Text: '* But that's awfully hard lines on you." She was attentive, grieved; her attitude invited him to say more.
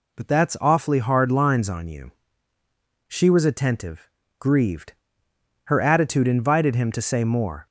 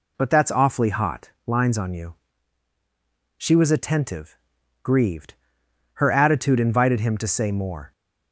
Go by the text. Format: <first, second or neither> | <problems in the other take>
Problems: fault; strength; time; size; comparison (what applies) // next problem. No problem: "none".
first | says "hot" for "hard"; at 0.8 s